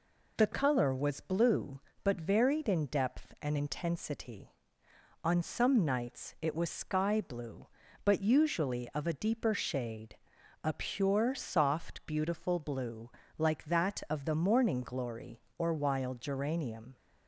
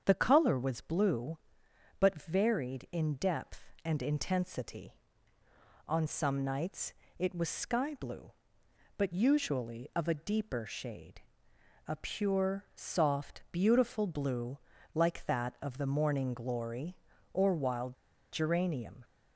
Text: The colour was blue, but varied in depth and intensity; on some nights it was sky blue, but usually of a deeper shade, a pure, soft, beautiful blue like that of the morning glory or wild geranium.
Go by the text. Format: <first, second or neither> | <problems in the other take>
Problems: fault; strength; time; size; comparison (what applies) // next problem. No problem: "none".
first | starts louder than the rest; strong; until 1.0 s; 7.5 dB // pauses between "nights" and "it"; slight; at 6.9 s; 0.26 s long // pauses between "blue" and "like"; slight; at 14.5 s; 0.36 s long; slight in the first // pauses between "wild" and "geranium"; at 17.9 s; 0.37 s long